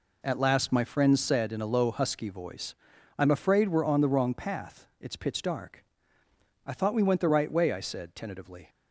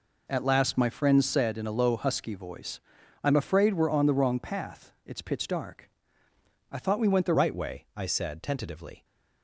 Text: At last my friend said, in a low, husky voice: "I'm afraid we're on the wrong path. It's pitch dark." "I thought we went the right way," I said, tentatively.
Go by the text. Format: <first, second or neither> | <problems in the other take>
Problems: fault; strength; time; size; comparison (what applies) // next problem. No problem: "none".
first | changes voice at "right"; from 7.3 s on; 1.7 s long